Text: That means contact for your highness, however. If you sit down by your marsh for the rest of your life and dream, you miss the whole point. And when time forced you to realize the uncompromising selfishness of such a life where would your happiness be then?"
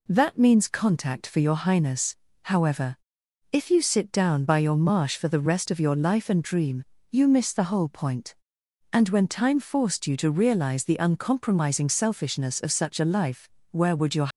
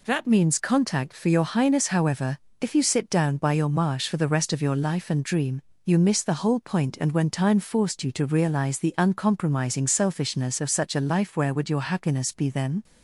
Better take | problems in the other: second | pauses between "life" and "where"; slight; at 13.4 s; 0.22 s long // stops before "happiness be then"; at 14.2 s

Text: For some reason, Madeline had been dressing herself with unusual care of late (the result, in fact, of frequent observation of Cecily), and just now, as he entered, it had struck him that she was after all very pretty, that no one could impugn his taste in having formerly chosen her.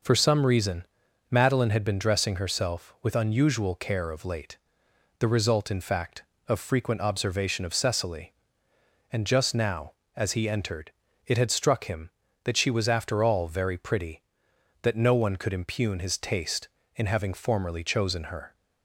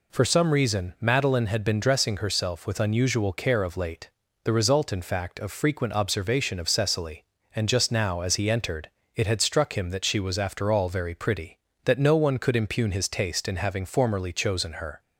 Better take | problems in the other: neither | none

